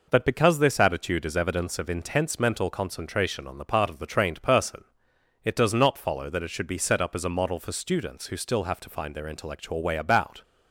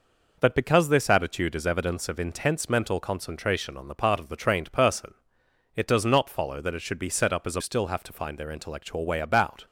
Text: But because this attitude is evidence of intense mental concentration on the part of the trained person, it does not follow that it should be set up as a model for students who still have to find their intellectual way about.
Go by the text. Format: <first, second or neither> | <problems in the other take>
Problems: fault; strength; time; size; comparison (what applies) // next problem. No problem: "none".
first | skips "model for students who"; at 7.5 s